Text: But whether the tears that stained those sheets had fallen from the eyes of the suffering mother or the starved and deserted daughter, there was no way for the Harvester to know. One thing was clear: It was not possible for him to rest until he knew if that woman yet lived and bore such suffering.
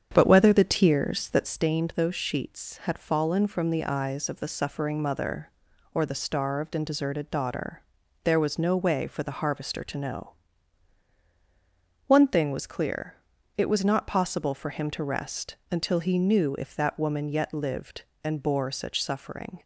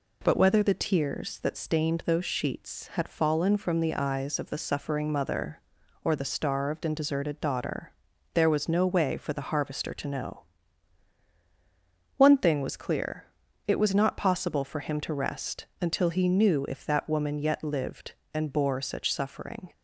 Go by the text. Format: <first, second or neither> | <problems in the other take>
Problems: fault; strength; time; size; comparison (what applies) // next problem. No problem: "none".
second | starts louder than the rest; strong; until 1.7 s; 8 dB